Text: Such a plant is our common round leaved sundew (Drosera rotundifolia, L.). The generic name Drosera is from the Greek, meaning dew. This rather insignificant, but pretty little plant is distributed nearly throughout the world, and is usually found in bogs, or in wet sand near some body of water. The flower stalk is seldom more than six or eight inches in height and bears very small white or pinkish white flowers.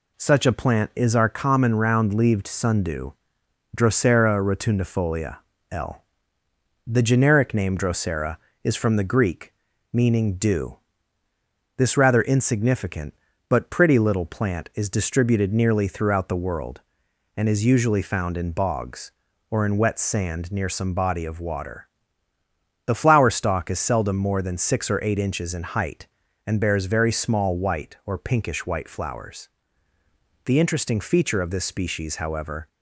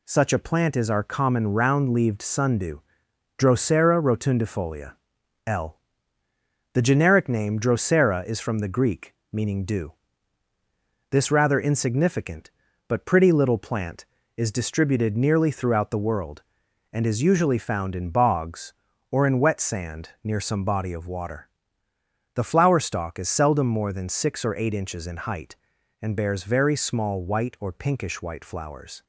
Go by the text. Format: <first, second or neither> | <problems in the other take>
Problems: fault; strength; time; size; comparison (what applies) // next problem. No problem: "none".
second | goes on to say "The interesting feature of this species however"; strong; from 30.4 s on; 2.2 s long